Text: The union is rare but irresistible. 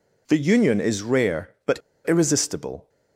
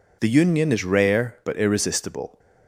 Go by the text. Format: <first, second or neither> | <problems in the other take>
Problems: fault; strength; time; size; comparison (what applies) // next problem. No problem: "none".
second | pauses between "but" and "irresistible"; slight; at 1.7 s; 0.29 s long